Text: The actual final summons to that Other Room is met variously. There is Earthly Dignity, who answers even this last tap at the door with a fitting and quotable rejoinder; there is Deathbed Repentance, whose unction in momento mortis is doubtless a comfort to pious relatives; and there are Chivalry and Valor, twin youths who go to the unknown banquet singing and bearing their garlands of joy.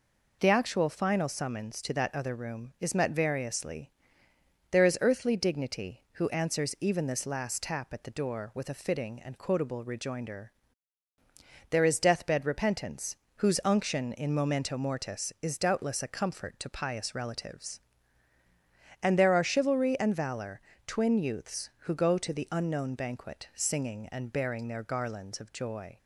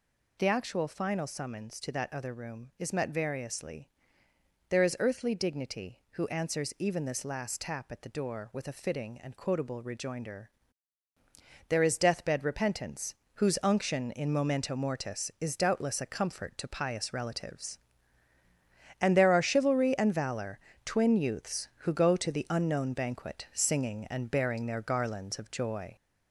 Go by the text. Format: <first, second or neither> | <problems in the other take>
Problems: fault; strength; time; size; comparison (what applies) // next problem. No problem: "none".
first | gets louder; noticeable; throughout; 4 dB